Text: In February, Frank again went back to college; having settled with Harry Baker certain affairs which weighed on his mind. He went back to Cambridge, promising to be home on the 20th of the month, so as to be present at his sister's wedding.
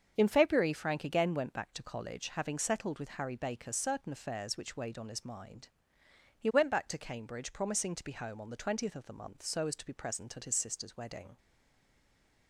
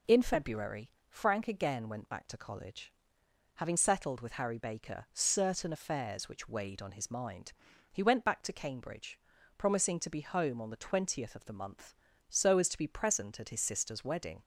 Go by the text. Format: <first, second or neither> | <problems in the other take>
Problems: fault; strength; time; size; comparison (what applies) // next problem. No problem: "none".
second | starts louder than the rest; until 1.1 s; 7 dB // stays silent after the last word; from 11.3 s on; 1.1 s long